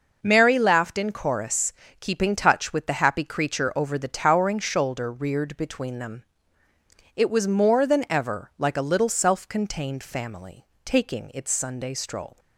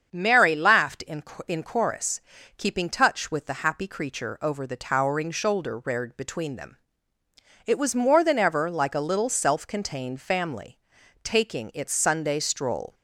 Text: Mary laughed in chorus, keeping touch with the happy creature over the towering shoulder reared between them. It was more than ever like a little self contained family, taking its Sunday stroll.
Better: first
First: none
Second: starts louder than the rest; strong; until 1.1 s; 7 dB // says "in" twice; at 1.4 s

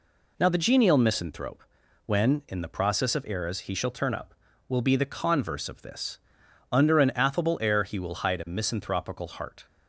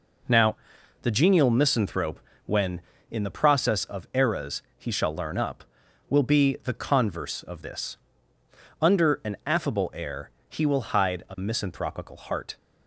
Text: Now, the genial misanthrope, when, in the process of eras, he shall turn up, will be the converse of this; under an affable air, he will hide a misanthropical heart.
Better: first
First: none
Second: says "learn" for "turn"; at 5.1 s

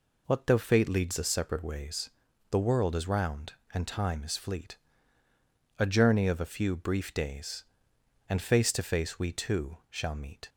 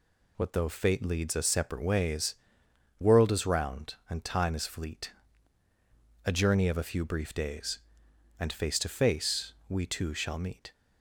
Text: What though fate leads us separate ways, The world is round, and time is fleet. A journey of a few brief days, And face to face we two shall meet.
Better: first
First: none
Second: skips "The"; at 2.6 s // pauses between "face" and "we"; slight; at 9.5 s; 0.16 s long

